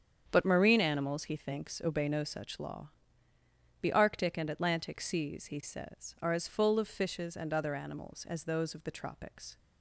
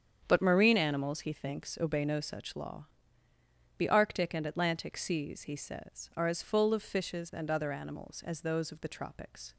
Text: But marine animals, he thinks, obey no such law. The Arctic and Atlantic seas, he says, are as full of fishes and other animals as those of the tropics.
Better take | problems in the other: neither | starts louder than the rest; strong; the same in both

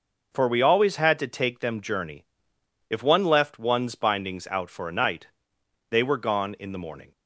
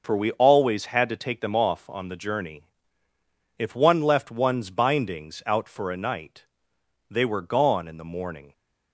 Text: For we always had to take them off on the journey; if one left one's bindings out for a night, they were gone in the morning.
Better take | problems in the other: second | skips "off on the"; at 1.8 s

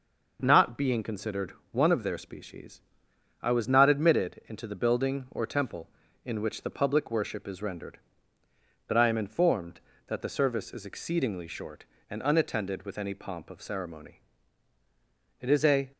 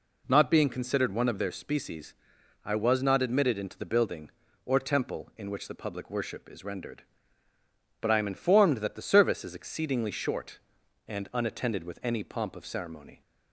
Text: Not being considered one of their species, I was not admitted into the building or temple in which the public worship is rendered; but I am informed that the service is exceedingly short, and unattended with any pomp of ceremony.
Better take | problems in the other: second | pauses between "considered" and "one"; slight; at 1.5 s; 0.18 s long // goes on to say "It is a"; from 15.4 s on; 0.50 s long

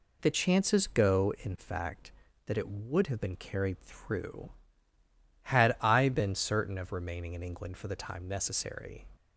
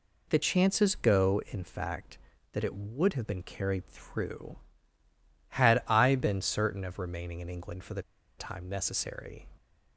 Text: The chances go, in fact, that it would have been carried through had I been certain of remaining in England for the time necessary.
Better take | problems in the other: first | pauses between "the" and "time"; at 8.0 s; 0.36 s long

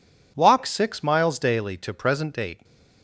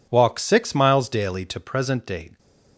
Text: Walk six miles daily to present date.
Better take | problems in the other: neither | none

